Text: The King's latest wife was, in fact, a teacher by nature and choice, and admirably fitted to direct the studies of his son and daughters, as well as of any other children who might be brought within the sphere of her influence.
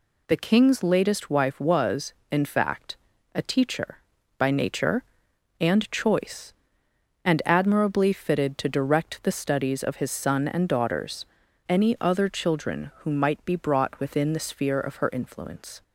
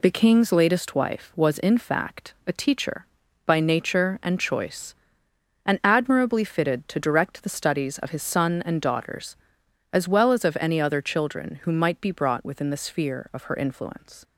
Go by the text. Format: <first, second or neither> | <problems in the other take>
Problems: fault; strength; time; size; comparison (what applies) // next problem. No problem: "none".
second | skips "as well as of"; at 11.4 s